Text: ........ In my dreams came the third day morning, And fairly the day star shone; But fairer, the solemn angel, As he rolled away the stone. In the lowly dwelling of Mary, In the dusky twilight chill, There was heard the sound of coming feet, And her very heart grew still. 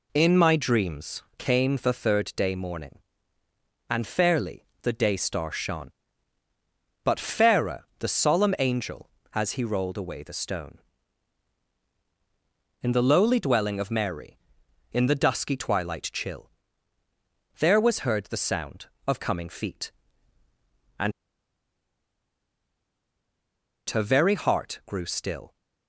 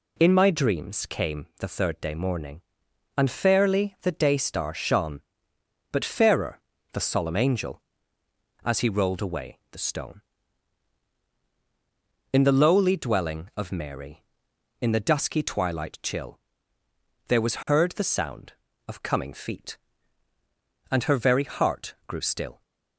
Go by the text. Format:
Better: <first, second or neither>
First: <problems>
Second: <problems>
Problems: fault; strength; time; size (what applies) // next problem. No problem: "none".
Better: second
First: pauses between "fairly" and "the"; slight; at 4.6 s; 0.16 s long // pauses between "And" and "her"; strong; at 21.1 s; 2.7 s long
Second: none